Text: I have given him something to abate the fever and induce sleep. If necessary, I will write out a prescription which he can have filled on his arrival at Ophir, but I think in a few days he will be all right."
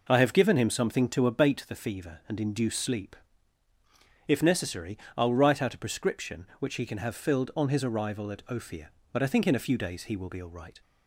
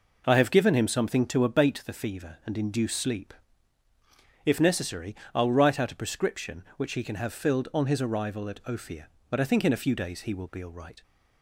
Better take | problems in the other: neither | none

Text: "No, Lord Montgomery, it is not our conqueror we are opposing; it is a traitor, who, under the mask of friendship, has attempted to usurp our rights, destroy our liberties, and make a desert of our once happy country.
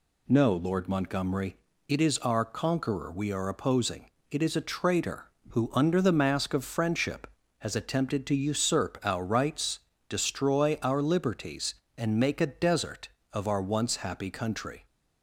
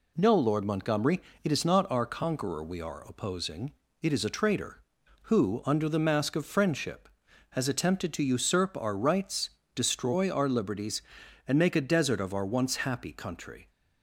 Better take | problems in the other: second | skips "not"; at 2.1 s

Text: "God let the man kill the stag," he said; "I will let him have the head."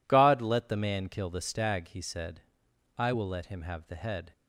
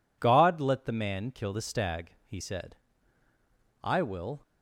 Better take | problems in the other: first | stops before "let him have the head"; at 4.4 s

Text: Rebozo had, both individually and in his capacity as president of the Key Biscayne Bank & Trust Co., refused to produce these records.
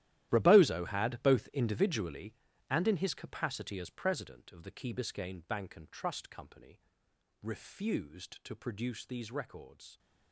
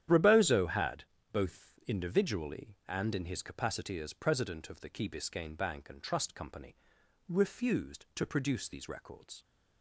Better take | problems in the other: second | gets quieter; strong; throughout; 16.5 dB // starts louder than the rest; strong; until 1.3 s; 13.5 dB; strong in the second

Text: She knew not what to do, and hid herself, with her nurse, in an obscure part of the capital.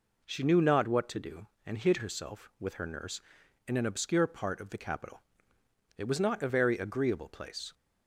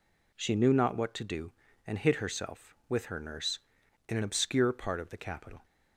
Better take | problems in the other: second | goes on to say "It was not a very agreeable place"; strong; from 5.9 s on; 1.7 s long

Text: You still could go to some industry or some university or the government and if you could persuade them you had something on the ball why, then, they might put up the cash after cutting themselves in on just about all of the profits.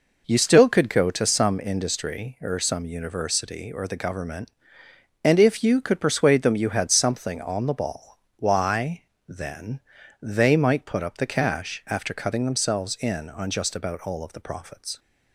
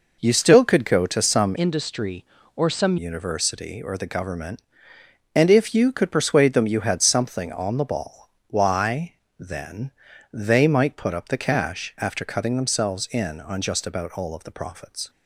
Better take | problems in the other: first | changes voice from "industry" to "some"; from 1.5 to 2.9 s; 1.4 s long // pauses between "ball" and "why"; slight; at 8.2 s; 0.18 s long; slight in the first

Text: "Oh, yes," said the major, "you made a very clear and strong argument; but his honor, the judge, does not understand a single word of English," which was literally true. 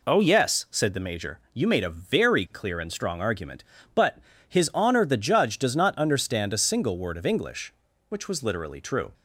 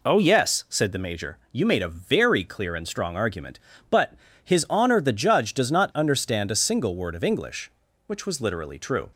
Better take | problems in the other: neither | pauses between "but" and "his"; slight; the same in both

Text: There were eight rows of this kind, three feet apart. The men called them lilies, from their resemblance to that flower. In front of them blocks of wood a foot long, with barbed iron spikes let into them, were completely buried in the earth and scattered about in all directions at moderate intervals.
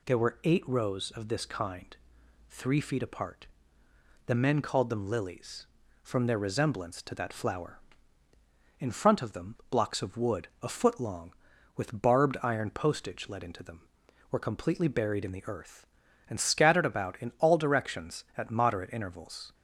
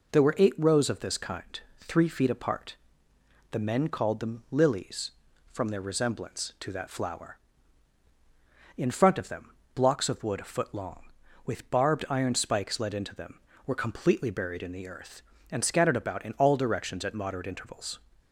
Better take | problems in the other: second | pauses between "them" and "blocks"; slight; at 9.5 s; 0.16 s long; slight in the second // says "postage" for "spikes"; at 12.6 s

